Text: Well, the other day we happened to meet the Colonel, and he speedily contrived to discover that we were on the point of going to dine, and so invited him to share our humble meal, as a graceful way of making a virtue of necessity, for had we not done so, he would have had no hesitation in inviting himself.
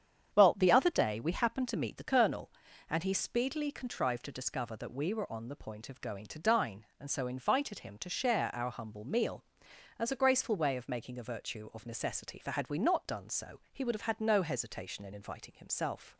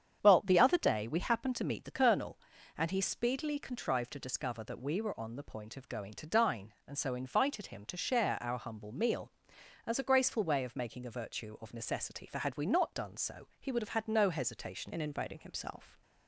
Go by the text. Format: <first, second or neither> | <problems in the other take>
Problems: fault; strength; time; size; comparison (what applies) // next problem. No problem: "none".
first | starts louder than the rest; strong; until 1.2 s; 8.5 dB; strong in the first // changes voice at "in"; from 14.9 s on; 1.1 s long